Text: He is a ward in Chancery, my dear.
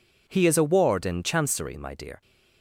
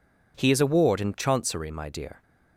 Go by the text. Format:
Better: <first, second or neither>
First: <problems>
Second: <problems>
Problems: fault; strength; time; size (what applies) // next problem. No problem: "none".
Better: neither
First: none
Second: none